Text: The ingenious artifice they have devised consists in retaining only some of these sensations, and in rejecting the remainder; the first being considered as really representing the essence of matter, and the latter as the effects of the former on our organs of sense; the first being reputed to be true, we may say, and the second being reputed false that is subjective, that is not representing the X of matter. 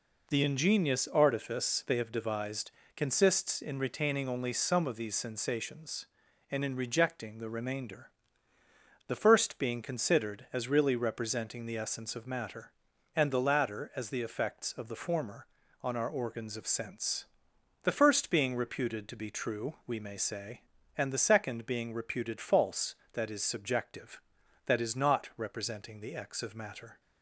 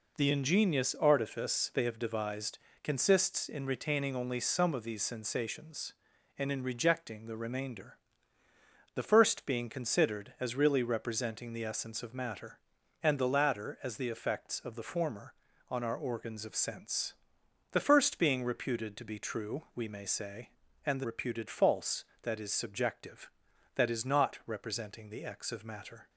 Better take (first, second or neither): first